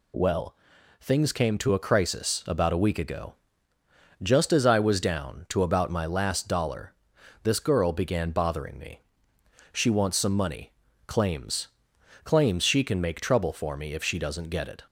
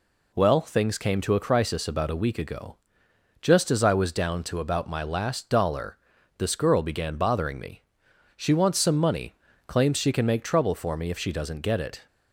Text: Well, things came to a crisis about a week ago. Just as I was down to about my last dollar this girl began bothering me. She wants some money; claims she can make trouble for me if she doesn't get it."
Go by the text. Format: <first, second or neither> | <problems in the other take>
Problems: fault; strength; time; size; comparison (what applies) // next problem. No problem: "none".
second | pauses between "dollar" and "this"; noticeable; at 6.9 s; 0.50 s long; also in the second // says "claims" twice; at 12.2 s